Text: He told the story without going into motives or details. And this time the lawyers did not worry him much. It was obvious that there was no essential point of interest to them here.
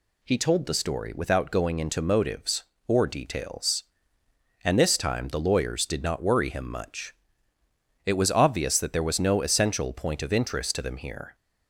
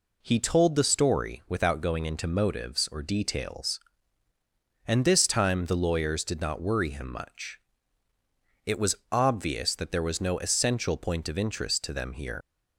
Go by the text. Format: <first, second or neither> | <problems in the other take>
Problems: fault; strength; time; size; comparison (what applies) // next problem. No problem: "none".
first | leaves "here" unfinished; at 12.4 s; 115 ms